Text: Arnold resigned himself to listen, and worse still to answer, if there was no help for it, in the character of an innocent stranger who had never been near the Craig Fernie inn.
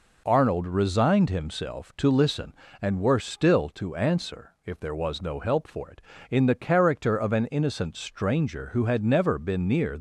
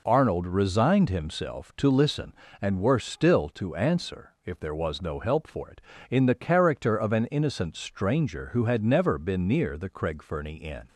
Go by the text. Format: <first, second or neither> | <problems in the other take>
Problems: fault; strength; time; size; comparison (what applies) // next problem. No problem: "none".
second | stops before "the Craig Fernie inn"; at 9.9 s